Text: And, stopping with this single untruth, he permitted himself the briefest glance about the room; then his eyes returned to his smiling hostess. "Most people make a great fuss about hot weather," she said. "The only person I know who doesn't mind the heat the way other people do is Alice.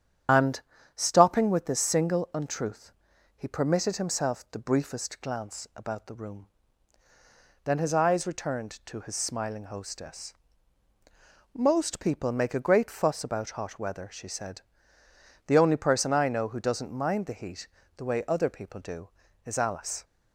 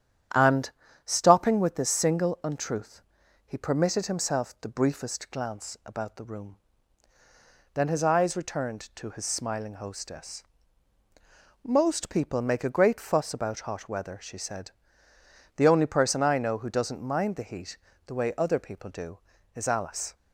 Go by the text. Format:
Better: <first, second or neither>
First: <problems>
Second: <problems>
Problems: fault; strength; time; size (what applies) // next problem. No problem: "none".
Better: second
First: loses the start of "And"; at 0.2 s; 80 ms // starts louder than the rest; strong; until 1.6 s; 9 dB // pauses between "heat" and "the"; slight; at 17.6 s; 0.30 s long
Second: starts louder than the rest; strong; until 1.6 s; 9.5 dB // pauses between "heat" and "the"; slight; at 17.7 s; 0.30 s long